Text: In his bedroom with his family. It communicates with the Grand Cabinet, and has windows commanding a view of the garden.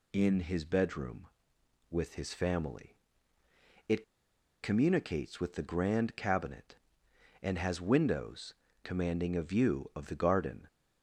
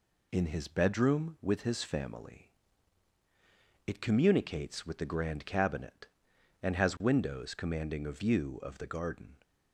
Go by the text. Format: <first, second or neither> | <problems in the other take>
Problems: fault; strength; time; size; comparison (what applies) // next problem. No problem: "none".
second | pauses between "It" and "communicates"; noticeable; at 4.0 s; 0.58 s long // pauses between "windows" and "commanding"; slight; at 8.5 s; 0.30 s long